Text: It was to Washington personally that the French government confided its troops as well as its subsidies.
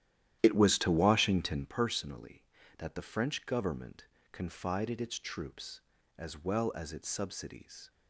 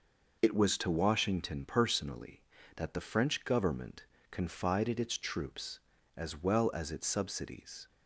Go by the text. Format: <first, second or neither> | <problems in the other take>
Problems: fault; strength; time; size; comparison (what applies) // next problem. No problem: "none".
second | starts louder than the rest; strong; until 1.7 s; 12 dB // pauses between "government" and "confided"; slight; at 4.0 s; 0.26 s long; slight in the second